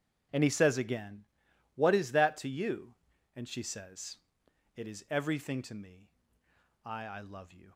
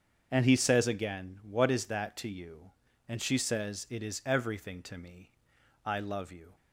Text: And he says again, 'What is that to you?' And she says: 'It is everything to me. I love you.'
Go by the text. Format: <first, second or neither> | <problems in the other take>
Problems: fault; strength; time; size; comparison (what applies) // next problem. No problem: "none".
second | starts louder than the rest; strong; until 1.8 s; 8 dB; also in the second // says "I" twice; at 7.0 s